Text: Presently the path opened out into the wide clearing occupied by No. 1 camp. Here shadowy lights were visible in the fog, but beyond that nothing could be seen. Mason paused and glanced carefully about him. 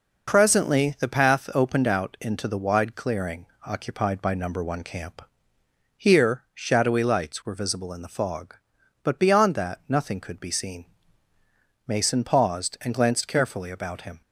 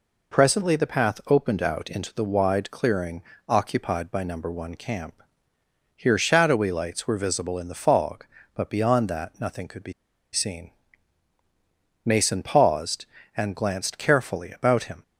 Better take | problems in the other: first | pauses between "clearing" and "occupied"; slight; at 3.2 s; 0.26 s long; slight in the first // pauses between "be" and "seen"; at 9.9 s; 0.40 s long

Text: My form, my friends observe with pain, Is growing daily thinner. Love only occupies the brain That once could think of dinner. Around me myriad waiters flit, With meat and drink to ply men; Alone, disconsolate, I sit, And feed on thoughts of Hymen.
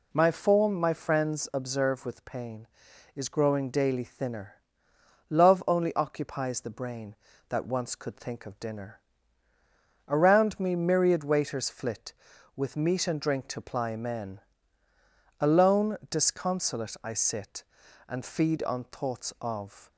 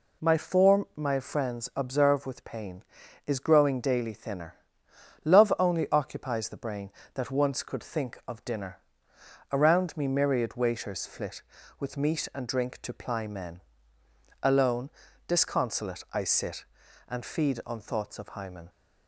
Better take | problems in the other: second | stops before "Hymen"; at 19.9 s

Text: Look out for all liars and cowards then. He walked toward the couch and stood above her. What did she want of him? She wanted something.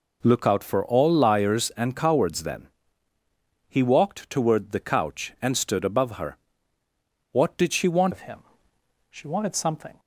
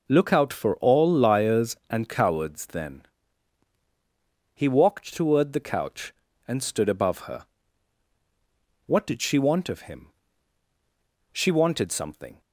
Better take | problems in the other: second | changes voice at "of"; from 8.1 s on; 1.8 s long

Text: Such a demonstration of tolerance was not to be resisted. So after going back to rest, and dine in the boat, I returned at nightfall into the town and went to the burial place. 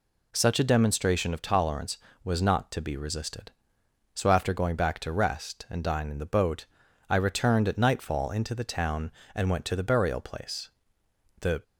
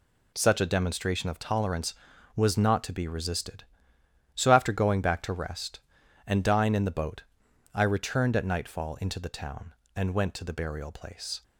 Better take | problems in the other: second | goes on to say "The"; slight; from 11.4 s on; 0.22 s long

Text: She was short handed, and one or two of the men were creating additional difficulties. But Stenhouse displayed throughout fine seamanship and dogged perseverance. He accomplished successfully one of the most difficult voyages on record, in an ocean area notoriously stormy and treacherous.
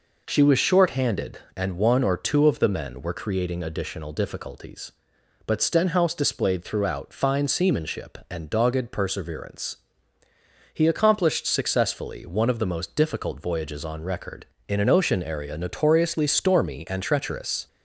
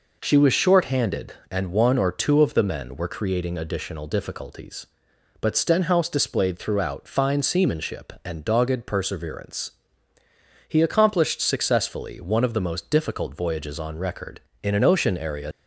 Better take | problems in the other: first | stops before "notoriously stormy and treacherous"; at 15.5 s

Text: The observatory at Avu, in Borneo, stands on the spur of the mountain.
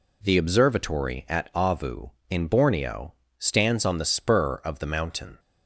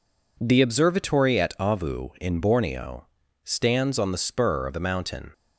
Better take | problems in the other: neither | none

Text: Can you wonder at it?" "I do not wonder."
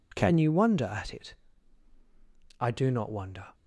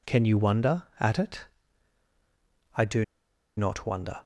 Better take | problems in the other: first | pauses between "do" and "not"; noticeable; at 3.0 s; 0.53 s long

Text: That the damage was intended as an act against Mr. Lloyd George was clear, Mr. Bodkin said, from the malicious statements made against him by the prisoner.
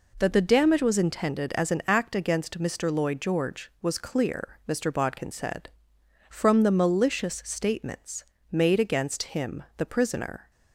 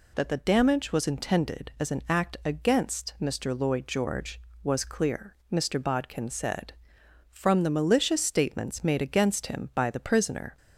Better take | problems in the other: second | pauses between "statements" and "made"; slight; at 8.2 s; 0.28 s long // skips "by"; at 9.7 s

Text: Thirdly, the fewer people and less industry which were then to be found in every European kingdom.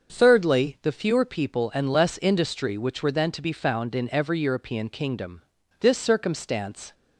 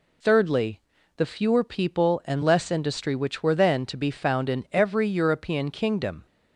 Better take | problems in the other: second | starts louder than the rest; until 1.1 s; 6.5 dB // goes on to say "This circumstance"; noticeable; from 5.8 s on; 1.1 s long

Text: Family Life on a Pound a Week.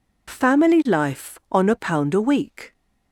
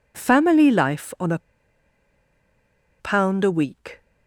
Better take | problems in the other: first | pauses between "a" and "Pound"; strong; at 1.3 s; 1.6 s long

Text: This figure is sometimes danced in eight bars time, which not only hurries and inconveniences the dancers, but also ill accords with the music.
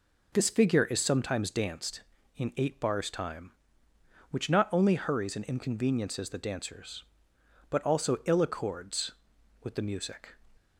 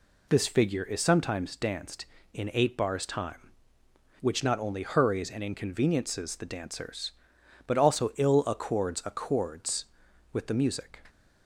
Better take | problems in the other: first | says "accords" twice; at 9.0 s

